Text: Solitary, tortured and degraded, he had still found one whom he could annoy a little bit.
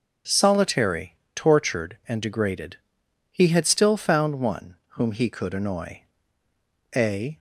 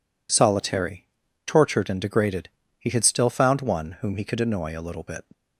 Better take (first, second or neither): second